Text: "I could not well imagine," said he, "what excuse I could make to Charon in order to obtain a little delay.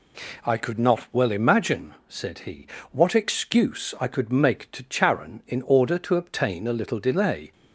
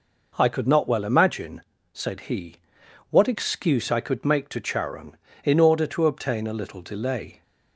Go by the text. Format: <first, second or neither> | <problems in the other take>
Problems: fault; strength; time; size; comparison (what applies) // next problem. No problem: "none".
neither | none